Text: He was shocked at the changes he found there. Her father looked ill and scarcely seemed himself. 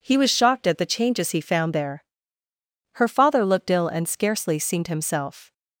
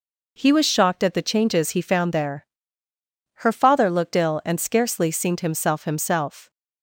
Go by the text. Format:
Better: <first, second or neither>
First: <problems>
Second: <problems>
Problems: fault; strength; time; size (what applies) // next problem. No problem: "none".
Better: first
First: none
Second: says "himself" twice; at 5.8 s